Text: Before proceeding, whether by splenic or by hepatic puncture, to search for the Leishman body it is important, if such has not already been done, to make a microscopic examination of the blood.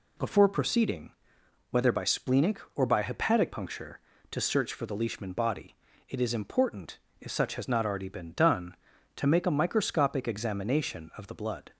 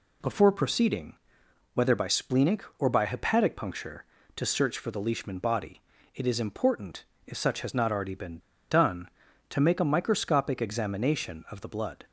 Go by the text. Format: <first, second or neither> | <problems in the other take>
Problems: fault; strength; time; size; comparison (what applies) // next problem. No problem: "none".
first | pauses between "body" and "it"; slight; at 5.8 s; 0.32 s long; slight in the first // pauses between "been" and "done"; slight; at 8.3 s; 0.31 s long